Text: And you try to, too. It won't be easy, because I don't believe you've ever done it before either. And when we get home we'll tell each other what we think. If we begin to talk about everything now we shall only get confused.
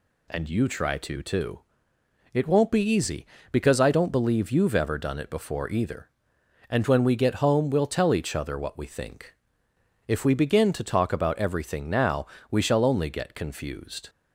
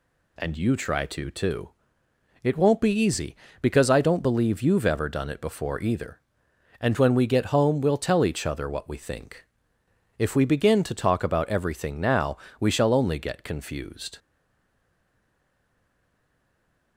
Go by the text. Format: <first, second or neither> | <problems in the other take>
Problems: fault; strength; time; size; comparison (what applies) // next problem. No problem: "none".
first | pauses between "now" and "we"; slight; at 12.3 s; 0.22 s long; slight in the first // stays silent after the last word; strong; from 14.1 s on; 2.8 s long